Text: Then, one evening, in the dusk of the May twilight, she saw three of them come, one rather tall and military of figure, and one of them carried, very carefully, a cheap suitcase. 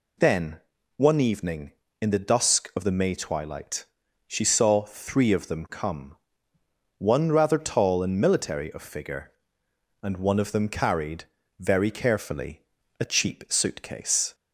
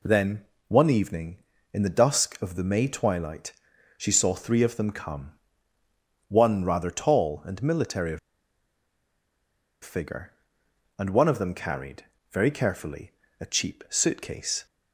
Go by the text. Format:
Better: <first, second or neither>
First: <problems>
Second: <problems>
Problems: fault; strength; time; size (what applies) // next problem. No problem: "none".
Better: first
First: none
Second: pauses between "of" and "figure"; strong; at 8.1 s; 1.6 s long